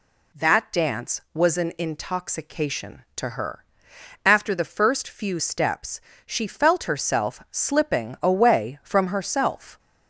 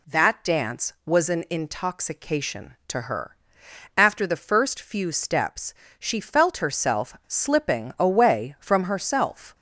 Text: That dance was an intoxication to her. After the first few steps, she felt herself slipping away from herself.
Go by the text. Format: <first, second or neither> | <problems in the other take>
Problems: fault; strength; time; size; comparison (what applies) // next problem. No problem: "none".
neither | none